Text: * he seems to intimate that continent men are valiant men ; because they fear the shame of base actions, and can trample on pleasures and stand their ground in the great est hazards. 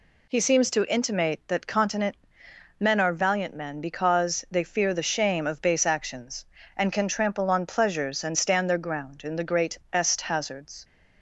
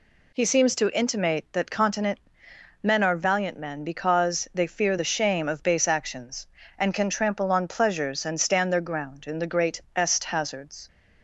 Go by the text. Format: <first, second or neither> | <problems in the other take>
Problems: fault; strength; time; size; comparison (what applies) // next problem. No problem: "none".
neither | pauses between "continent" and "men"; noticeable; the same in both